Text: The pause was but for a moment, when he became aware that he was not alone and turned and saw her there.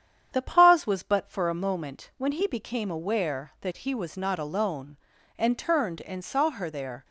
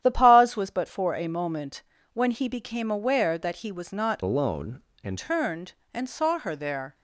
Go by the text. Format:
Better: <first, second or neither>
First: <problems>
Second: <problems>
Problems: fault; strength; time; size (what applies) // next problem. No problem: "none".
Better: first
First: starts louder than the rest; strong; until 1.3 s; 8.5 dB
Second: starts louder than the rest; strong; until 1.0 s; 10.5 dB // changes voice from "alone" to "and"; from 4.2 to 5.1 s; 0.9 s long